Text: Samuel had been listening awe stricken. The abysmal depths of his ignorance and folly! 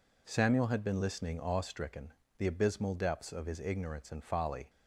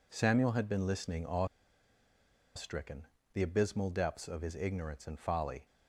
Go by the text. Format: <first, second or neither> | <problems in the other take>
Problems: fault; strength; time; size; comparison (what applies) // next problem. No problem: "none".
first | pauses between "awe" and "stricken"; at 1.4 s; 1.1 s long